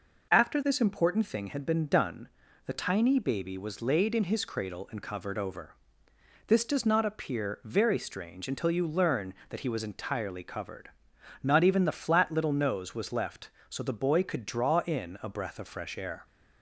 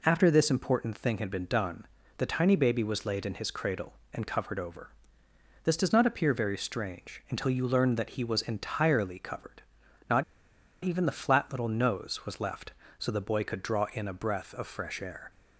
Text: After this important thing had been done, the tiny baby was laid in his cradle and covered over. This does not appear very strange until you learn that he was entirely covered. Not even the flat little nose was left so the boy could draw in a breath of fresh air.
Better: first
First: none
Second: pauses between "Not" and "even"; noticeable; at 10.2 s; 0.58 s long

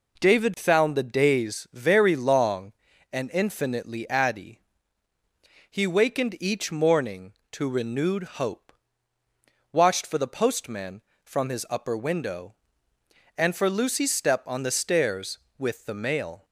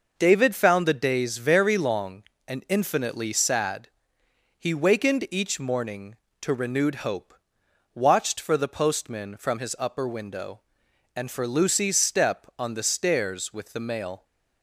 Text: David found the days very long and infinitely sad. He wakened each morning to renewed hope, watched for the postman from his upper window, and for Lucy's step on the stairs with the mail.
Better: second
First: says "addy" for "sad"; at 4.0 s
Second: none

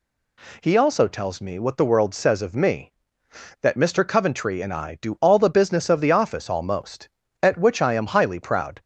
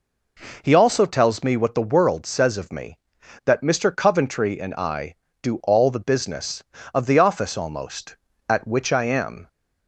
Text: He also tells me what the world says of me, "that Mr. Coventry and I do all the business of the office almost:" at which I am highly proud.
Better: first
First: none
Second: stops before "highly proud"; at 9.4 s

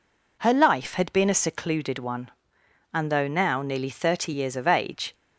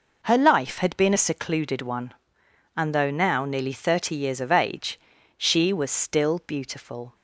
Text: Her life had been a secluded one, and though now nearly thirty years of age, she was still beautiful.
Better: second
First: stops before "she was still beautiful"; at 5.1 s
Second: none

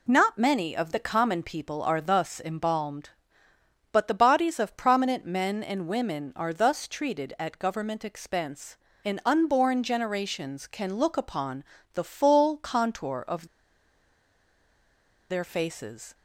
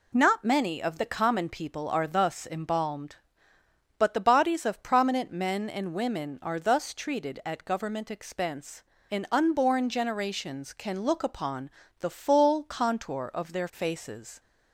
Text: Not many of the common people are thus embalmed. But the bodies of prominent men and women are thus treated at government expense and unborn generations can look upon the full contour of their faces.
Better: second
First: pauses between "upon" and "the"; slight; at 11.6 s; 0.30 s long // pauses between "of" and "their"; strong; at 13.4 s; 1.8 s long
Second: pauses between "upon" and "the"; slight; at 11.6 s; 0.30 s long

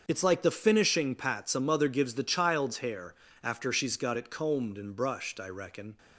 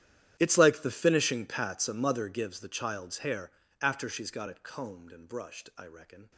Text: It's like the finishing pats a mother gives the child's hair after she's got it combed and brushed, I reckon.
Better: first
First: starts louder than the rest; until 1.0 s; 7 dB // pauses between "hair" and "after"; slight; at 3.1 s; 0.30 s long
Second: gets quieter; strong; throughout; 21 dB // starts louder than the rest; strong; until 1.4 s; 11.5 dB // pauses between "hair" and "after"; slight; at 3.5 s; 0.32 s long

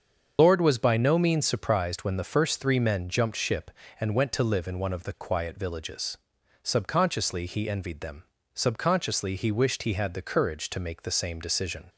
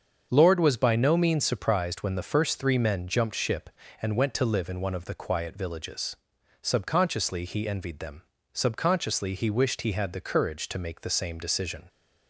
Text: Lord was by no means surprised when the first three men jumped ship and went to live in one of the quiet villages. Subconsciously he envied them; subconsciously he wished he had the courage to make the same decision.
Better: second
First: loses the start of "Lord"; at 0.3 s; 65 ms // starts louder than the rest; until 1.3 s; 7 dB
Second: starts louder than the rest; until 1.3 s; 7 dB

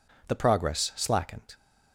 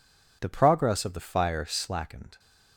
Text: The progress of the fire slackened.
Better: second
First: skips "of the fire"; at 0.9 s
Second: none

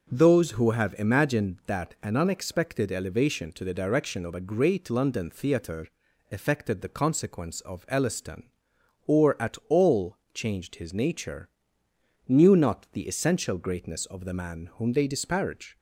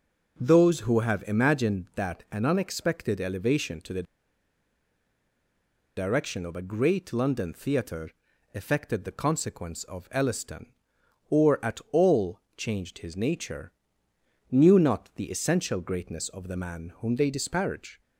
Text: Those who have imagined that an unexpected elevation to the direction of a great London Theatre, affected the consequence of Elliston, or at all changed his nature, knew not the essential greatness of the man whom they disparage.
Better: first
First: pauses between "all" and "changed"; slight; at 10.1 s; 0.16 s long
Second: pauses between "the" and "direction"; strong; at 4.0 s; 1.9 s long // pauses between "all" and "changed"; slight; at 12.4 s; 0.16 s long

